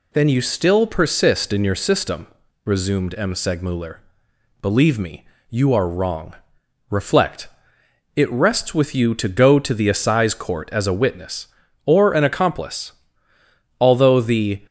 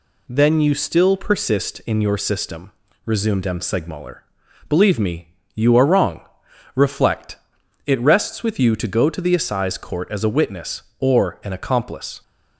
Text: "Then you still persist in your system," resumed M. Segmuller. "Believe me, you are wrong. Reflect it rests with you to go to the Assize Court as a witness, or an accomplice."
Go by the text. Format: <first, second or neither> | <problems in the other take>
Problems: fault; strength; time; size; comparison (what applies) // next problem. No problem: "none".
second | pauses between "Reflect" and "it"; noticeable; at 7.4 s; 0.66 s long; noticeable in the second // goes on to say "Although the"; noticeable; from 13.7 s on; 0.82 s long